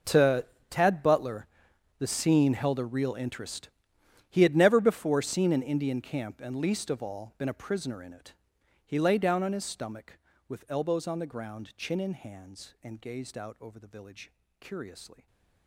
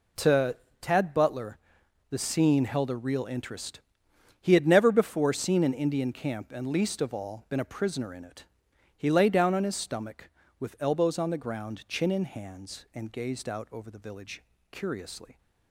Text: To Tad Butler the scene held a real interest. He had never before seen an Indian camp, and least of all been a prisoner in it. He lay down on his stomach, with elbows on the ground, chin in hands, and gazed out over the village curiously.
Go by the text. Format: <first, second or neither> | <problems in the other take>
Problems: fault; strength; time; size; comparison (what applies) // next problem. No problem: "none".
second | gets quieter; strong; throughout; 18 dB // pauses between "To" and "Tad"; slight; at 0.4 s; 0.24 s long; slight in the second // pauses between "Butler" and "the"; noticeable; at 1.4 s; 0.52 s long; noticeable in the second // pauses between "village" and "curiously"; slight; at 14.3 s; 0.30 s long; slight in the second